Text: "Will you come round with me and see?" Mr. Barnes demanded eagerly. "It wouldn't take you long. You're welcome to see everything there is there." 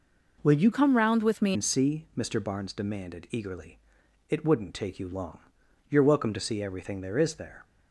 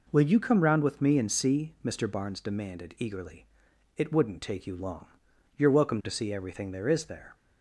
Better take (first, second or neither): second